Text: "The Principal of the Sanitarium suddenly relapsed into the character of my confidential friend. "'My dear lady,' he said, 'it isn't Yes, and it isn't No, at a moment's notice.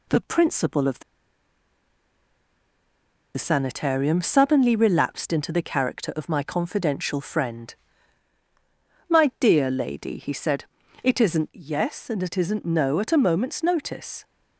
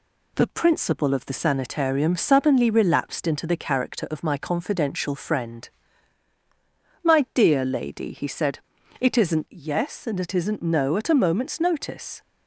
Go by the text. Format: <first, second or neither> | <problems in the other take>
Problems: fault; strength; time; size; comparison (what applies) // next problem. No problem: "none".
second | pauses between "the" and "Sanitarium"; strong; at 1.0 s; 2.3 s long